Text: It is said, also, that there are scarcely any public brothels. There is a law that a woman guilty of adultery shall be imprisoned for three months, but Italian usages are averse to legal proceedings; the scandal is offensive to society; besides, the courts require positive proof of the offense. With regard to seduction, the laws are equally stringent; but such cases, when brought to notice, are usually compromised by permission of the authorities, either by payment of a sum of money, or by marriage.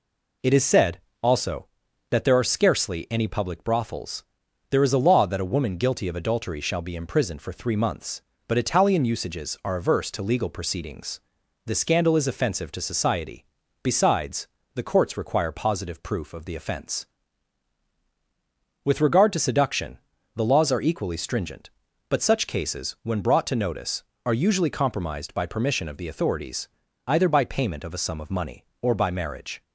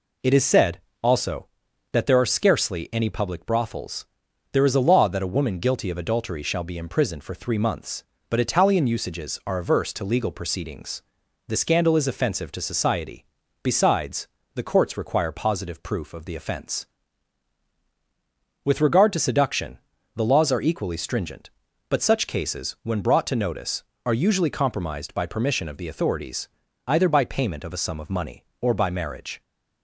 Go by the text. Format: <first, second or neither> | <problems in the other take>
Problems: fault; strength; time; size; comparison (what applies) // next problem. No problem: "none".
neither | none